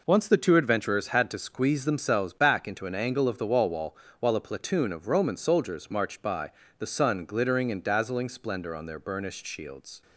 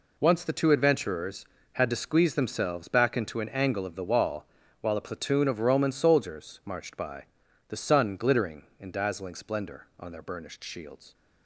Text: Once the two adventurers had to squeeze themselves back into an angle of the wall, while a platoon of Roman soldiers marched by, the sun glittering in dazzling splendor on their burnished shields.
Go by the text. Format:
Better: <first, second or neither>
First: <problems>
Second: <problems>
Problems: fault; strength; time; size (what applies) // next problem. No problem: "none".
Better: second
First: says "wall" twice; at 3.6 s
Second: none